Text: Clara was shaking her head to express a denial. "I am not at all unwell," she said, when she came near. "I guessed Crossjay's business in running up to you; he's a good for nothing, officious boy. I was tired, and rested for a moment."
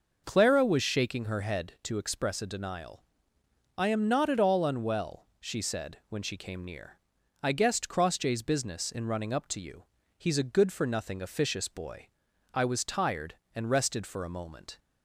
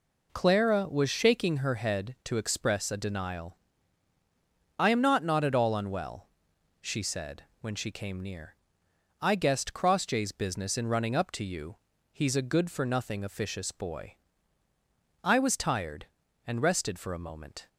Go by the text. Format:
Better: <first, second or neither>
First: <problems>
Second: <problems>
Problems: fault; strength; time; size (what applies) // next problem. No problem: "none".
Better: first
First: none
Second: says "not" twice; at 5.2 s